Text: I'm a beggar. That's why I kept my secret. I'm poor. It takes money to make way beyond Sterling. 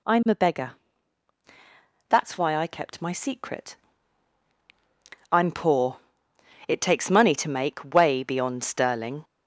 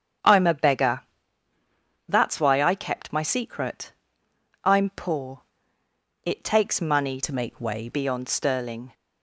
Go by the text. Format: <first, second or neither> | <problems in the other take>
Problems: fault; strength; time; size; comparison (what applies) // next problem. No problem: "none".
first | starts louder than the rest; strong; until 2.2 s; 8 dB // changes voice from "to" to "way"; from 7.2 to 7.8 s; 0.6 s long